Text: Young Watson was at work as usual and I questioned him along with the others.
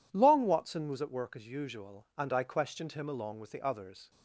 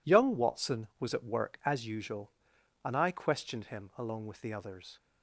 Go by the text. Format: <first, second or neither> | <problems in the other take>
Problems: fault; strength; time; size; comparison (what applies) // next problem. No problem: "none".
second | says "Long" for "Young"; at 0.1 s